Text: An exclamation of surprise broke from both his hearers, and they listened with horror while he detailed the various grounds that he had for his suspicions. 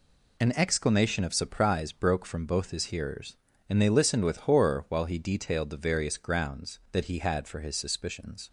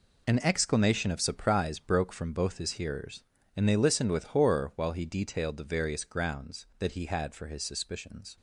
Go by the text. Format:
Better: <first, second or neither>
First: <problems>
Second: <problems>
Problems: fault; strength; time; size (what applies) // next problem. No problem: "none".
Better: first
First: none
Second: gets quieter; strong; throughout; 10.5 dB